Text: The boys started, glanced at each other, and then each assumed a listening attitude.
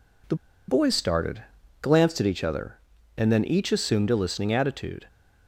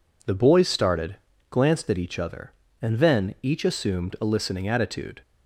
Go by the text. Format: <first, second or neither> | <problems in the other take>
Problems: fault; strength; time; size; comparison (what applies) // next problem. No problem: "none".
second | pauses between "The" and "boys"; slight; at 0.3 s; 0.33 s long